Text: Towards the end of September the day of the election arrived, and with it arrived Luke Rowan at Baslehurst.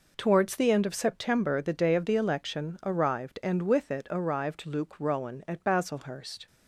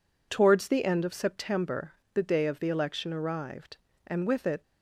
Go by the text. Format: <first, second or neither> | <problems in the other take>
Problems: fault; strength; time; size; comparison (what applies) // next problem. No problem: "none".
first | pauses between "September" and "the"; slight; at 1.9 s; 0.22 s long // stops before "arrived Luke Rowan at Baslehurst"; at 4.6 s